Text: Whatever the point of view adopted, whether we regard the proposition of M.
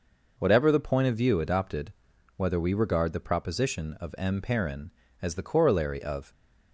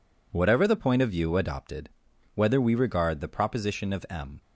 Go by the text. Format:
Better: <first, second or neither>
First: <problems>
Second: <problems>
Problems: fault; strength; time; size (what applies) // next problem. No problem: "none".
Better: second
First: goes on to say "Perrin as the corollary of"; strong; from 4.3 s on; 1.9 s long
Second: none